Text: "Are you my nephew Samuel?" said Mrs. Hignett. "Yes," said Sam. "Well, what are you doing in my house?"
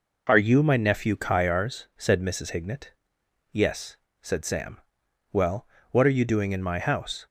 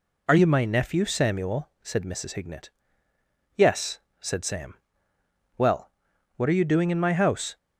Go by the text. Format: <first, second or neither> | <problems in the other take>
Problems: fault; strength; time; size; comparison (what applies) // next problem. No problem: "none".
second | says "Kyars" for "Samuel"; at 1.1 s